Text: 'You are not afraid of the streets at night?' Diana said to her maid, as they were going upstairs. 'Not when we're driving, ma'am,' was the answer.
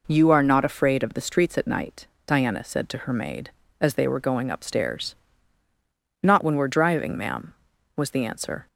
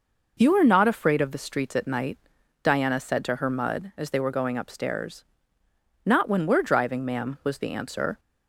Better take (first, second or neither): first